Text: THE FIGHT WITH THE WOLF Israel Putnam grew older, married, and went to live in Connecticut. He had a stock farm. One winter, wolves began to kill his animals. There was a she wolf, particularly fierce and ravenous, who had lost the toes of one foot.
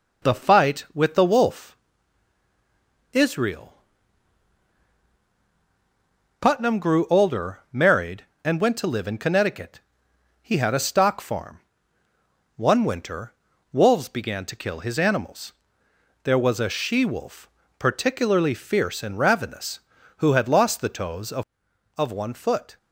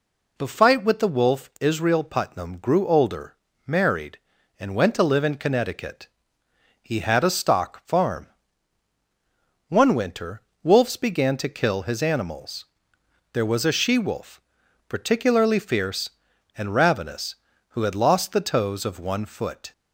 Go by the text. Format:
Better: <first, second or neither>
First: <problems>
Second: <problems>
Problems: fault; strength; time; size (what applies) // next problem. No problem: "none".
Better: second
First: pauses between "WOLF" and "Israel"; strong; at 1.7 s; 1.3 s long // pauses between "Israel" and "Putnam"; strong; at 3.7 s; 2.6 s long // says "of" twice; at 21.9 s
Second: none